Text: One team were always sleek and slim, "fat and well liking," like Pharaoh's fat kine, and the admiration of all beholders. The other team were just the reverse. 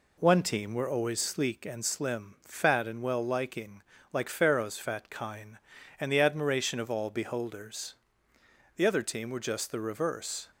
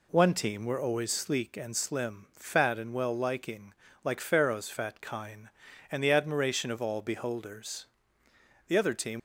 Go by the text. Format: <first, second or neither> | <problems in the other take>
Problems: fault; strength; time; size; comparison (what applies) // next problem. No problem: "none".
first | stops before "were just the reverse"; at 9.1 s